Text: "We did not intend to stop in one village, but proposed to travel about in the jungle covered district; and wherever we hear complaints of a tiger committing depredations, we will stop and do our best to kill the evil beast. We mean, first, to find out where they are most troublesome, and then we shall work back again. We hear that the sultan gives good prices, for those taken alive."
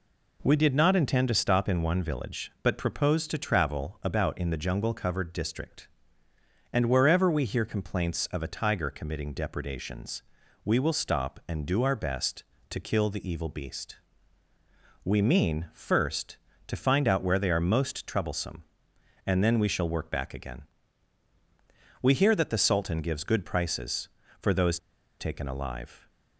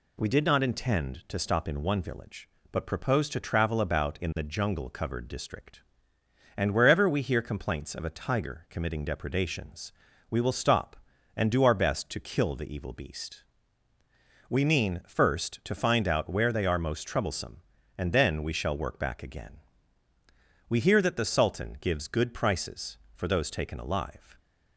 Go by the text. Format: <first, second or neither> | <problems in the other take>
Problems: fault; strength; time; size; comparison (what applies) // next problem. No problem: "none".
second | pauses between "those" and "taken"; at 24.7 s; 0.40 s long